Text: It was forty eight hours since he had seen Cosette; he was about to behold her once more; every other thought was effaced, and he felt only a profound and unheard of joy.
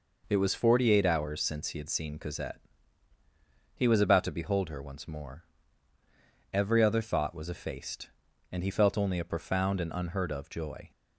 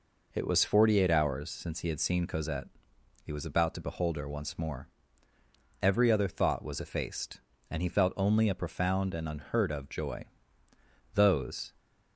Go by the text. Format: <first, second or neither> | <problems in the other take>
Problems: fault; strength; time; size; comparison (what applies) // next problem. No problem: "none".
first | goes on to say "Those"; from 11.1 s on; 0.58 s long